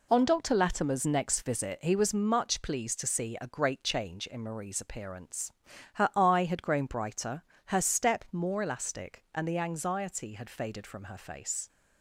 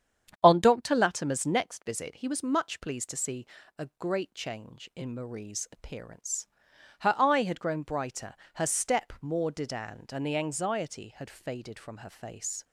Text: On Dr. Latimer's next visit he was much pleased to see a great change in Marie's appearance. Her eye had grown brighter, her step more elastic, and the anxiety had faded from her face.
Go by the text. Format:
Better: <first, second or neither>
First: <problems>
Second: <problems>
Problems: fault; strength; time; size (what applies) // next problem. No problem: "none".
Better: first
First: none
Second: starts louder than the rest; strong; until 1.4 s; 8.5 dB // pauses between "see" and "a"; slight; at 3.4 s; 0.32 s long // says "didand" for "elastic"; at 9.5 s